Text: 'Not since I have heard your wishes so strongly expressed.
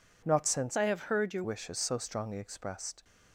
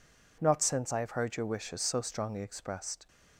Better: second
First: changes voice from "I" to "your"; from 0.7 to 1.4 s; 0.7 s long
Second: none

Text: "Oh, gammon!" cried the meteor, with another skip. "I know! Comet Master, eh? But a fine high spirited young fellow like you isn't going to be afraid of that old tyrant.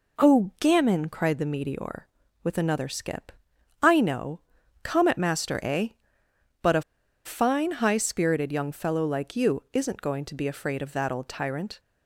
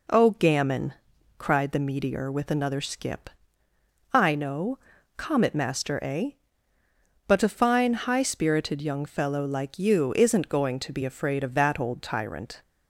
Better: second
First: pauses between "a" and "fine"; at 6.8 s; 0.43 s long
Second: none

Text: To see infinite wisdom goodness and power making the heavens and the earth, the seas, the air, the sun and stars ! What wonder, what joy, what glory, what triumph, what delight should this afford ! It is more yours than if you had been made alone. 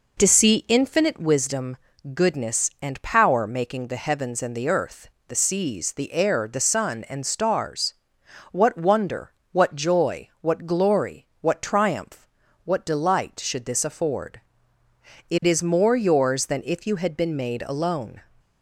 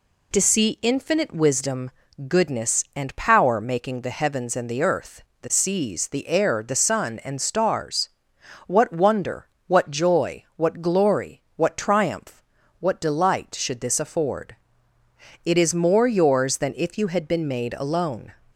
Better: second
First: starts louder than the rest; noticeable; until 1.2 s; 4.5 dB // pauses between "wisdom" and "goodness"; at 1.7 s; 0.38 s long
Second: pauses between "wisdom" and "goodness"; at 1.8 s; 0.38 s long

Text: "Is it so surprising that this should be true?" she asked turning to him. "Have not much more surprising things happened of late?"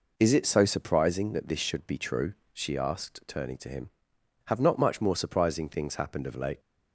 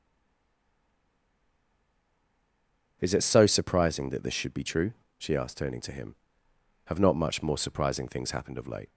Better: first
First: none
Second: stays silent before the first word; strong; until 3.0 s; 3.0 s long

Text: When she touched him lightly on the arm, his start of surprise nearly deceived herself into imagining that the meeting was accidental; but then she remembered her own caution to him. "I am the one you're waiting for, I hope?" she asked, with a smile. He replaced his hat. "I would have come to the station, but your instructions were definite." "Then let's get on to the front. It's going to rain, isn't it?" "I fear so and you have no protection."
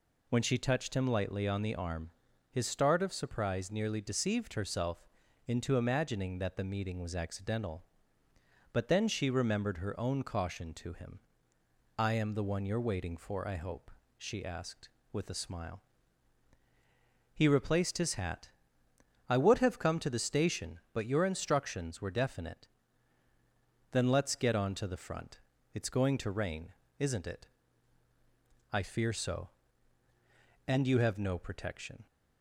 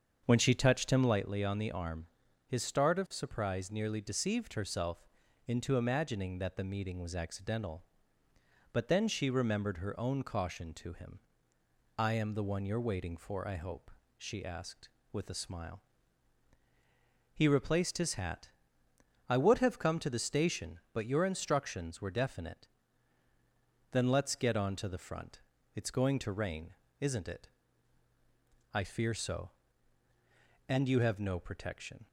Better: first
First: pauses between "herself" and "into"; at 5.0 s; 0.42 s long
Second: starts louder than the rest; until 1.3 s; 7 dB // pauses between "herself" and "into"; at 5.0 s; 0.42 s long

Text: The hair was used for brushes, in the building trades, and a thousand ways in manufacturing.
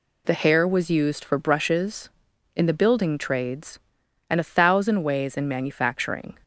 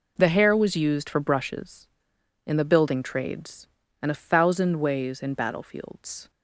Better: first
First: none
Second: says "battlefields" for "manufacturing"; at 5.3 s

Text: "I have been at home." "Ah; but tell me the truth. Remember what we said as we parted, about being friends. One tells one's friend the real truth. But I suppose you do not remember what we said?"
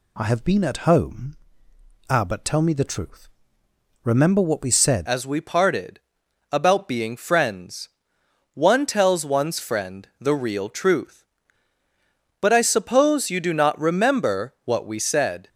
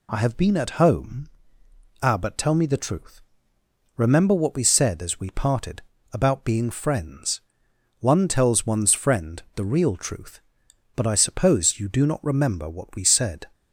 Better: second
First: changes voice at "as"; from 5.0 s on; 10.4 s long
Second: none

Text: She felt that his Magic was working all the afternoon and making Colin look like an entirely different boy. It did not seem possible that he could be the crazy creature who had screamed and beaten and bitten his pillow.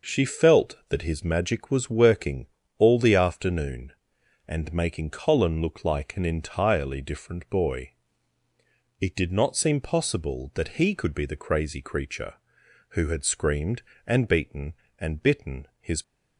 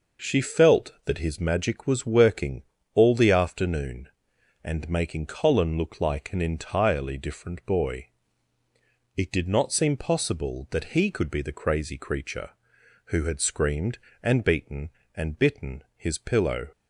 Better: second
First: pauses between "working" and "all"; slight; at 2.4 s; 0.30 s long // stops before "pillow"; at 16.0 s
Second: pauses between "working" and "all"; slight; at 2.6 s; 0.30 s long

